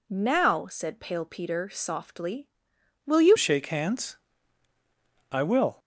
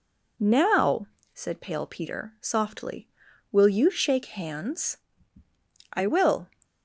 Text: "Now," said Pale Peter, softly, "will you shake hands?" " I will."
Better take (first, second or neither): second